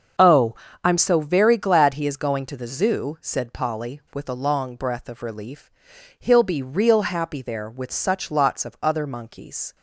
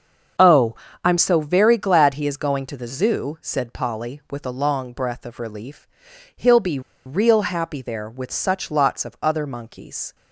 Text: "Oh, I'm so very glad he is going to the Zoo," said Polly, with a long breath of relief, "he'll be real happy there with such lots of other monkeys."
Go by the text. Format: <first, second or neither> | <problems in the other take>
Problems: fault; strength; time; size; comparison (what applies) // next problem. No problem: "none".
first | starts louder than the rest; until 1.7 s; 7 dB; also in the first // pauses between "be" and "real"; slight; at 6.7 s; 0.25 s long